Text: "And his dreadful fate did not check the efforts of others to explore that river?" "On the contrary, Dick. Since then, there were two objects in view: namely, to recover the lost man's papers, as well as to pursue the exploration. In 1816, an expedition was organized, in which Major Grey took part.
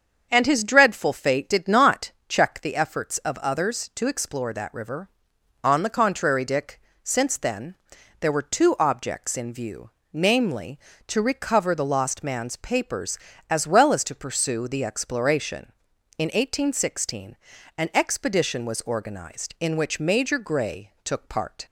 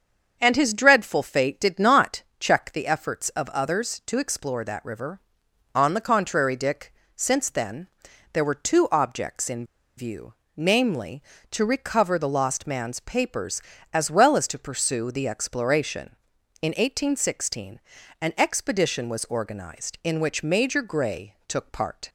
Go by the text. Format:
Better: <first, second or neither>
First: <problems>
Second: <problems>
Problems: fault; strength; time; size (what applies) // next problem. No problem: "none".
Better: first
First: starts louder than the rest; strong; until 1.3 s; 7 dB // pauses between "not" and "check"; slight; at 2.1 s; 0.18 s long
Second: starts louder than the rest; strong; until 1.4 s; 7 dB // pauses between "not" and "check"; slight; at 2.2 s; 0.18 s long // pauses between "in" and "view"; slight; at 9.6 s; 0.33 s long